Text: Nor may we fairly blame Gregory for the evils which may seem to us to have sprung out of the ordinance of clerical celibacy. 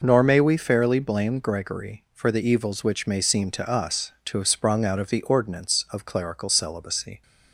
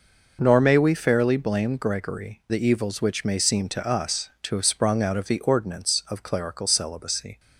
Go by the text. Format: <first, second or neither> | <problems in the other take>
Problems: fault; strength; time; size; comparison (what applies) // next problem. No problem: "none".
first | skips "for"; at 2.4 s